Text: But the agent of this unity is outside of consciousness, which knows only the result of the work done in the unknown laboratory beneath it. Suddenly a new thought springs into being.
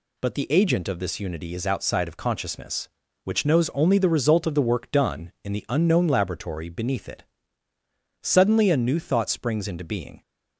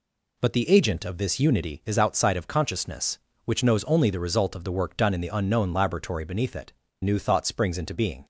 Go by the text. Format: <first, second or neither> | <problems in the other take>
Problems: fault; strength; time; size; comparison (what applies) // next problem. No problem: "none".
first | skips "Suddenly a"; at 6.8 s